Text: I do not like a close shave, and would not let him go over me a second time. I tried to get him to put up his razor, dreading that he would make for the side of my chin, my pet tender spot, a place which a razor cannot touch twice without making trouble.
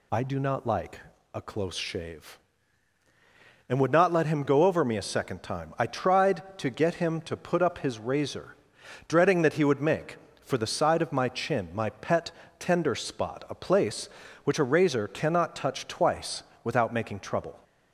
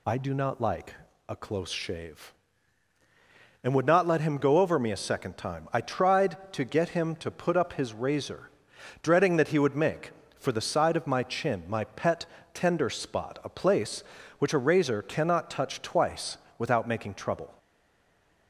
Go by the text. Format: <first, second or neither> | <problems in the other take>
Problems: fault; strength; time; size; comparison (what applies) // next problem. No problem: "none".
first | pauses between "like" and "a"; slight; at 0.9 s; 0.36 s long; slight in the first // pauses between "pet" and "tender"; slight; at 12.2 s; 0.26 s long; slight in the first // pauses between "twice" and "without"; slight; at 16.3 s; 0.22 s long; slight in the first // stays silent after the last word; slight; from 17.5 s on; 0.9 s long